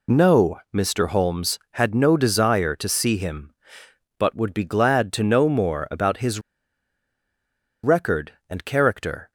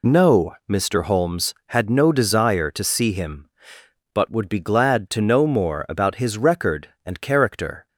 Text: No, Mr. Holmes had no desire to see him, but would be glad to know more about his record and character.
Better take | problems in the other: second | pauses between "his" and "record"; strong; at 6.3 s; 1.4 s long

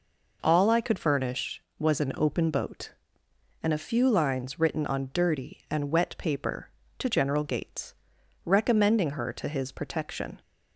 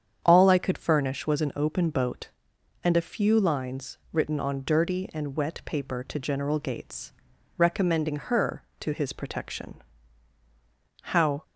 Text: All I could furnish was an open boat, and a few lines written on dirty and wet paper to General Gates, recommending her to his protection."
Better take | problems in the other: first | starts louder than the rest; strong; until 1.2 s; 8 dB // goes on to say "How"; slight; from 11.0 s on; 0.42 s long

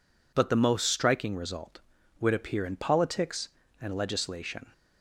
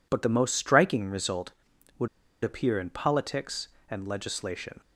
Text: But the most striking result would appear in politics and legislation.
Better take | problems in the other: first | pauses between "would" and "appear"; slight; at 2.0 s; 0.34 s long

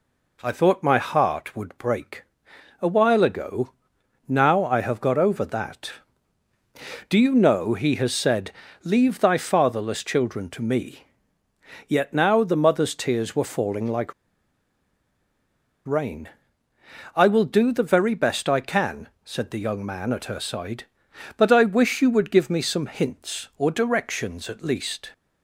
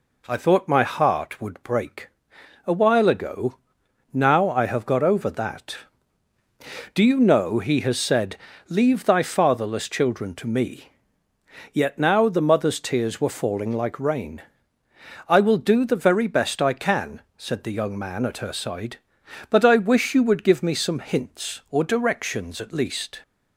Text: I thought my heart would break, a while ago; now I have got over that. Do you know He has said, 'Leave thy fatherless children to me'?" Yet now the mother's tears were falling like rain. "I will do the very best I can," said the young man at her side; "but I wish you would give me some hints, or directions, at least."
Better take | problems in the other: second | pauses between "like" and "rain"; strong; at 14.1 s; 1.7 s long

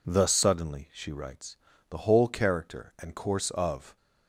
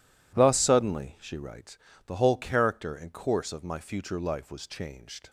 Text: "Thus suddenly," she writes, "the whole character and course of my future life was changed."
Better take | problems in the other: second | stops before "my future life was changed"; at 3.9 s

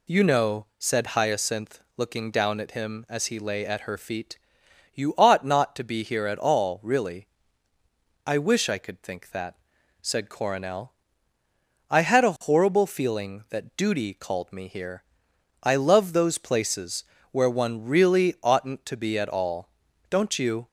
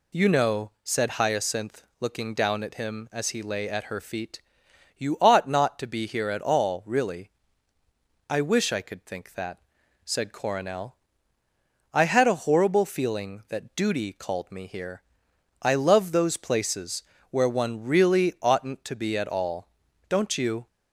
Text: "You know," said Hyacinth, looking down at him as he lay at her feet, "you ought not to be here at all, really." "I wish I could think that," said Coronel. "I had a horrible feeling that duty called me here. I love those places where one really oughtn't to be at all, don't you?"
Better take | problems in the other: neither | pauses between "places" and "where"; slight; the same in both

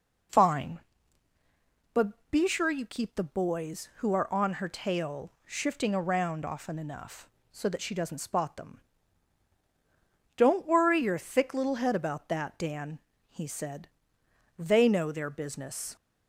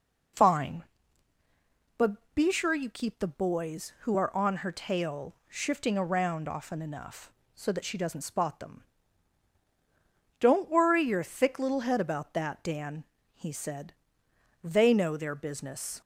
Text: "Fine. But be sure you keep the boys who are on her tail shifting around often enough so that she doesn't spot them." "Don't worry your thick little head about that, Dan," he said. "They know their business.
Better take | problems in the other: neither | none

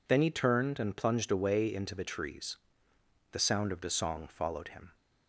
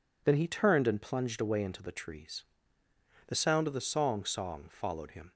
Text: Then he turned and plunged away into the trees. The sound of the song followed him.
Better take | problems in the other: first | says "song" twice; at 4.2 s

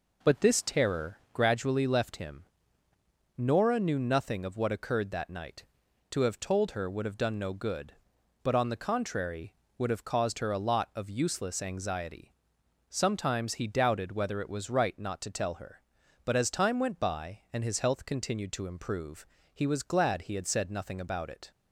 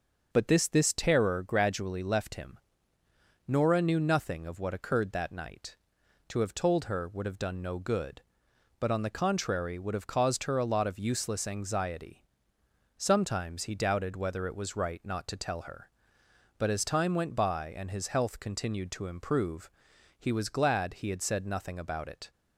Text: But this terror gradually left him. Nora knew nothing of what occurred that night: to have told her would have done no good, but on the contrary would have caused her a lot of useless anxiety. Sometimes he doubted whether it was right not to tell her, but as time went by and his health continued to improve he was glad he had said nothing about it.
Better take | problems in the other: first | says "this" twice; at 0.6 s // pauses between "improve" and "he"; noticeable; at 19.6 s; 0.48 s long; slight in the first

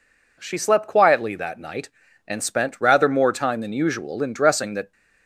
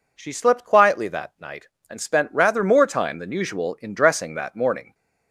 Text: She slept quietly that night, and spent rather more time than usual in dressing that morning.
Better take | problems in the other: second | stops before "morning"; at 4.9 s

